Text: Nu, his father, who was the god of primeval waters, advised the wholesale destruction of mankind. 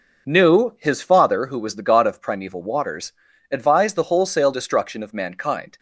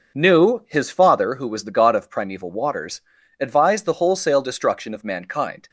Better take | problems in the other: neither | none

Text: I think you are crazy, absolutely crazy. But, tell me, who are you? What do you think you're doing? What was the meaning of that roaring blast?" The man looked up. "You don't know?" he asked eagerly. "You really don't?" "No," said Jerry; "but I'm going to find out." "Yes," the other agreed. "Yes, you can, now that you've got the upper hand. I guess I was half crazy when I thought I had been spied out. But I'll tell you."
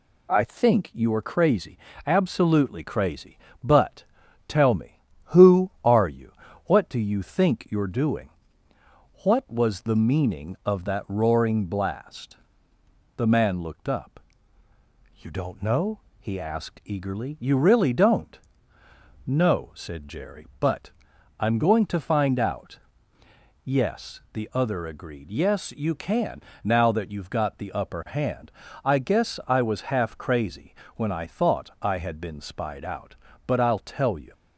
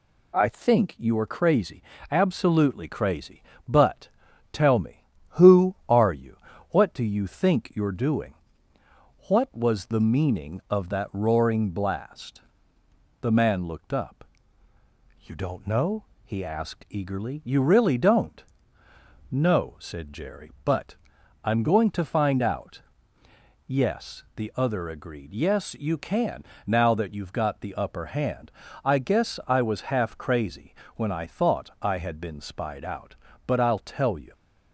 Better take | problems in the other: neither | pauses between "but" and "I'm"; noticeable; the same in both // pauses between "crazy" and "when"; slight; the same in both

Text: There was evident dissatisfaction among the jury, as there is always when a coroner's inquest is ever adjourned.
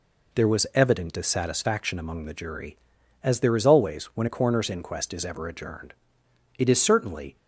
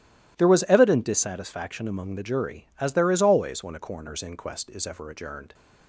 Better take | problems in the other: second | goes on to say "It is certainly"; noticeable; from 6.5 s on; 0.78 s long

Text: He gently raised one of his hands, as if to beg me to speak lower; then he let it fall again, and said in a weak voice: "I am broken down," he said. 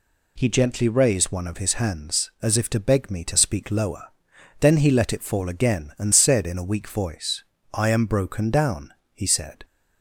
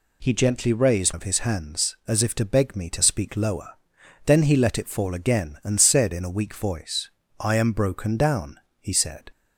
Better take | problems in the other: first | skips "one"; at 1.1 s

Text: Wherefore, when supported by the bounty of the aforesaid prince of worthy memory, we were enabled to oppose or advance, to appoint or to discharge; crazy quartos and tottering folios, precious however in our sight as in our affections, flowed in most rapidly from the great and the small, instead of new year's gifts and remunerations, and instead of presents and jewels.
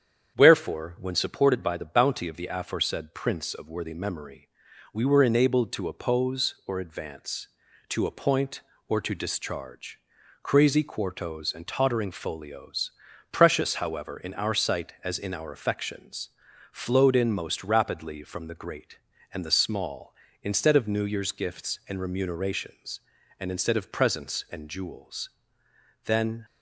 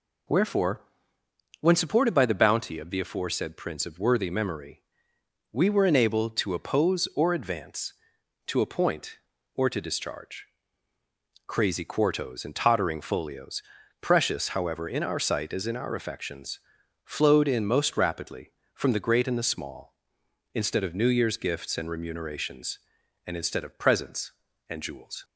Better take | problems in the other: second | starts louder than the rest; strong; until 1.4 s; 8 dB // goes on to say "Then"; slight; from 26.0 s on; 0.40 s long

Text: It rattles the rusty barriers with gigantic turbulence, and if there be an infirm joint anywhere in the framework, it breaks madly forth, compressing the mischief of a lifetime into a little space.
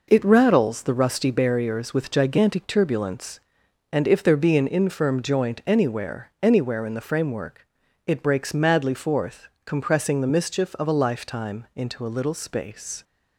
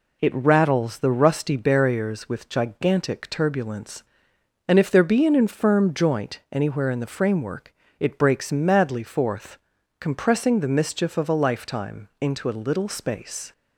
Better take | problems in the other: second | says "anywhere" twice; at 6.4 s

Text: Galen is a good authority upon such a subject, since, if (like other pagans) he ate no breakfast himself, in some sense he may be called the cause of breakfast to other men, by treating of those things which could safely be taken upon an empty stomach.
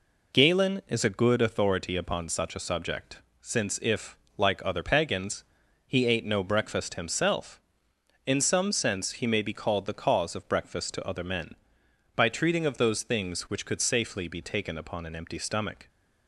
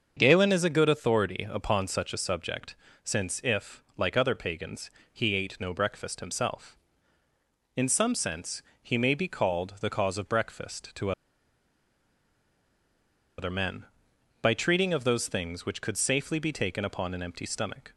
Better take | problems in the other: first | starts louder than the rest; until 1.1 s; 6.5 dB // pauses between "sense" and "he"; slight; at 8.6 s; 0.18 s long // pauses between "to" and "other"; strong; at 11.1 s; 2.2 s long

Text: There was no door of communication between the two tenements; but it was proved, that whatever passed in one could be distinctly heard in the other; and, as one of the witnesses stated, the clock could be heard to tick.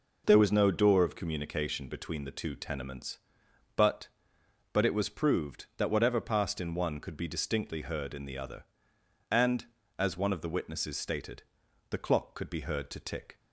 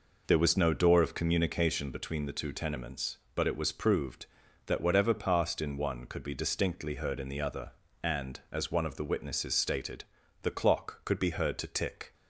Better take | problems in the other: second | says "but" twice; at 4.7 s

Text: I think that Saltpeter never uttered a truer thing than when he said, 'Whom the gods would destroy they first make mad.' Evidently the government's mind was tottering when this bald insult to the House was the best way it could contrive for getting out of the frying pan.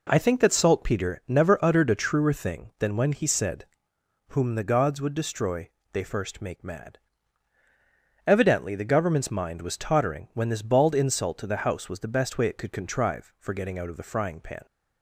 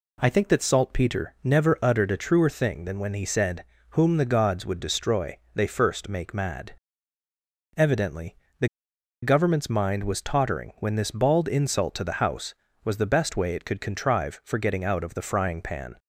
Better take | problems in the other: first | pauses between "destroy" and "they"; slight; at 5.3 s; 0.18 s long; slight in the first // pauses between "Evidently" and "the"; slight; at 8.3 s; 0.24 s long // pauses between "the" and "government's"; noticeable; at 8.6 s; 0.55 s long

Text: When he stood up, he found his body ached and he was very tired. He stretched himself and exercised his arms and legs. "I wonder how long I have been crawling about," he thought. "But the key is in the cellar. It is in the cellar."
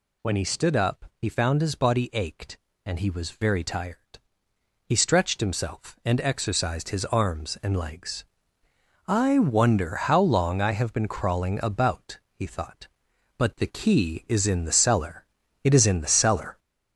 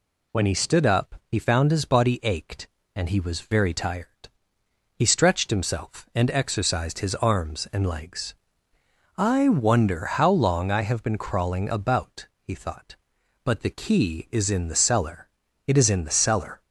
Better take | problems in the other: second | gets louder; noticeable; throughout; 4 dB

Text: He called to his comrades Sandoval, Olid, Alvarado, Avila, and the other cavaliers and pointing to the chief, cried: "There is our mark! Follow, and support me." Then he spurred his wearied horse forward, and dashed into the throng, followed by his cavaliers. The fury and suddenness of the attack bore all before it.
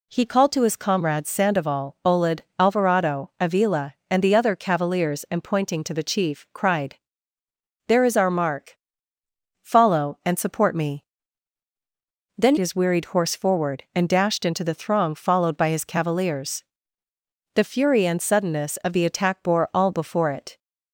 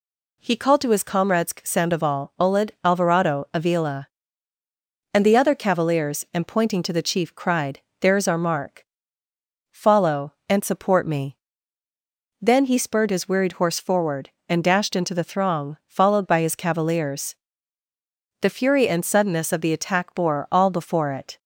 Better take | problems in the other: second | skips "he spurred"; at 12.5 s

